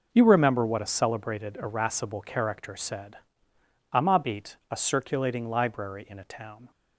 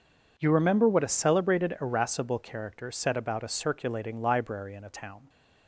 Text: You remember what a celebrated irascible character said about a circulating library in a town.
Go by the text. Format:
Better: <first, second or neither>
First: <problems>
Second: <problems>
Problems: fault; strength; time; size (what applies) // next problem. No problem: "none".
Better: second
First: says "amabit" for "about"; at 3.9 s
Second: none